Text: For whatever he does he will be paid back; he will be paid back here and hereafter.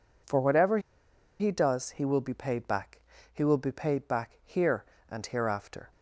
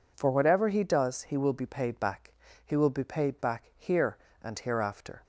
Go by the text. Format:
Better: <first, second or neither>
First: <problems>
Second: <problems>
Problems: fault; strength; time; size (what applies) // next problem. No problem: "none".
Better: second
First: pauses between "whatever" and "he"; noticeable; at 0.7 s; 0.61 s long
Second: none